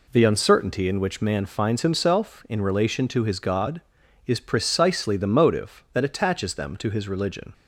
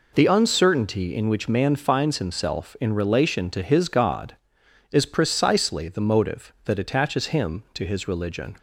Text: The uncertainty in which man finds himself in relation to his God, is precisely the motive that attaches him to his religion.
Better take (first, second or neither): second